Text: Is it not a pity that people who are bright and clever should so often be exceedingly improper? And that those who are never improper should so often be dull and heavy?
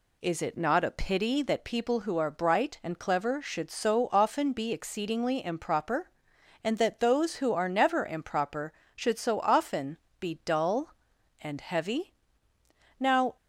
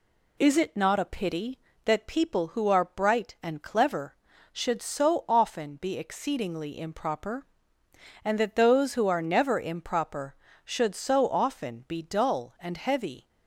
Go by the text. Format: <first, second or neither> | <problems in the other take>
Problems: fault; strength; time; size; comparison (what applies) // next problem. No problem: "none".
second | pauses between "often" and "be"; slight; at 9.9 s; 0.22 s long // goes on to say "Now"; slight; from 12.9 s on; 0.38 s long